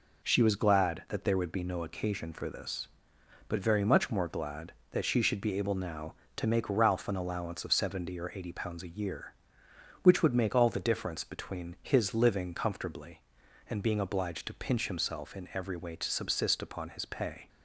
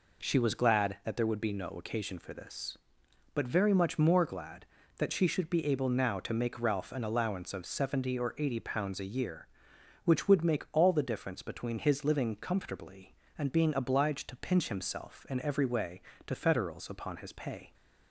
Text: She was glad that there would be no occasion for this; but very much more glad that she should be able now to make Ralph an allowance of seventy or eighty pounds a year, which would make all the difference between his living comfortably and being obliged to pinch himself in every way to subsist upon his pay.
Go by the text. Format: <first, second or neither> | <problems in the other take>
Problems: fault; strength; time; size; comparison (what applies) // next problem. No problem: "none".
first | says "federals" for "subsist"; at 16.3 s